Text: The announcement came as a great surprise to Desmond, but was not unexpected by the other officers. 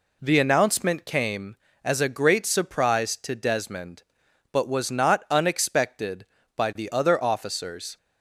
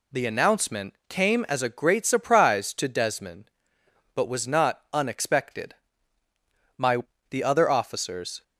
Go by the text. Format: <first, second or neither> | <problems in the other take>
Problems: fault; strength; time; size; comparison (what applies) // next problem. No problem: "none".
first | says "my" for "by"; at 6.7 s